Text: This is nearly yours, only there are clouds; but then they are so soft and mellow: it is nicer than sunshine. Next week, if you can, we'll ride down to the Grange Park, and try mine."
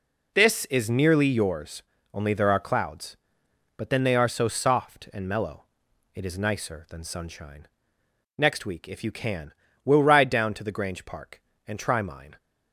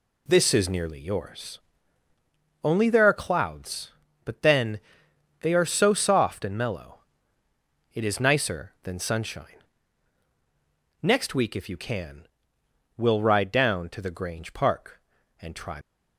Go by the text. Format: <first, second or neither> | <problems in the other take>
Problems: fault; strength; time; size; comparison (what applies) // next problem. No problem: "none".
first | pauses between "then" and "they"; noticeable; at 4.8 s; 0.58 s long // stops before "mine"; at 15.8 s